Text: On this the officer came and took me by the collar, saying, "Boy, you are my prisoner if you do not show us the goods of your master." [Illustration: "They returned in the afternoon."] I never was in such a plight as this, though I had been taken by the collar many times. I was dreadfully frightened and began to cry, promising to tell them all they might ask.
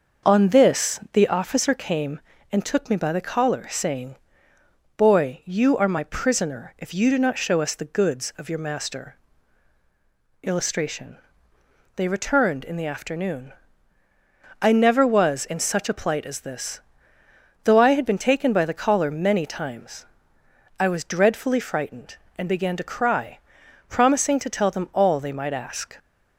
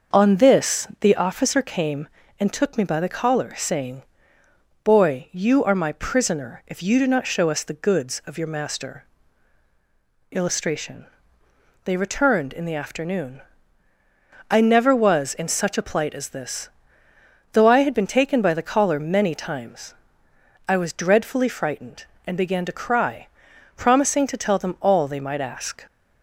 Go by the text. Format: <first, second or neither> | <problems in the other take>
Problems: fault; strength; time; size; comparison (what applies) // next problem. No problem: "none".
neither | starts louder than the rest; the same in both